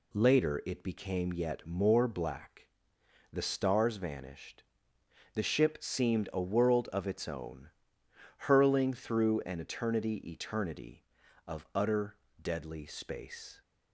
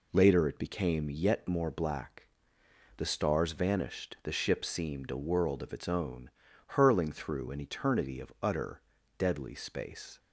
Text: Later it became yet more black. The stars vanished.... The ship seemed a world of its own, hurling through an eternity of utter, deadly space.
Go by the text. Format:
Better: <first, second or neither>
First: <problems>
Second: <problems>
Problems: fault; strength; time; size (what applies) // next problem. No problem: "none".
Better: second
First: says "eternity" twice; at 10.3 s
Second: none